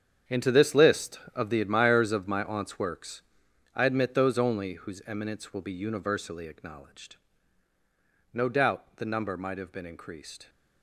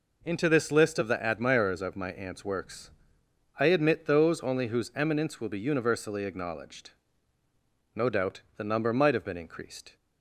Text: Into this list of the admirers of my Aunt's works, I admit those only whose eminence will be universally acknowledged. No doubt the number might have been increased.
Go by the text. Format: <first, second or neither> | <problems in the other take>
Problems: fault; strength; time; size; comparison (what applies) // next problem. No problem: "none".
second | gets quieter; strong; throughout; 13.5 dB